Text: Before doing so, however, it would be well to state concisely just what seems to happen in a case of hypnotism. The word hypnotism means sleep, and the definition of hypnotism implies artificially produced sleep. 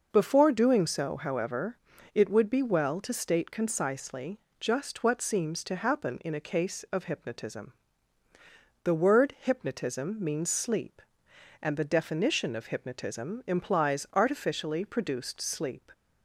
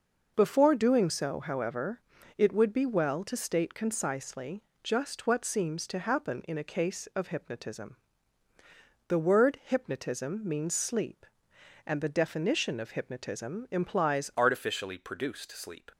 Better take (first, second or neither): first